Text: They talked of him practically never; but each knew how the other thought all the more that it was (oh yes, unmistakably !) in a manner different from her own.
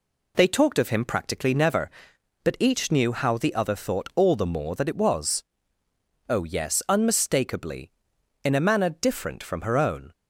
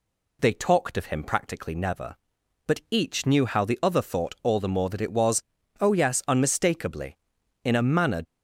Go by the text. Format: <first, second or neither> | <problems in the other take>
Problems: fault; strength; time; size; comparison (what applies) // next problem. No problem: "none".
first | stops before "different from her own"; at 8.2 s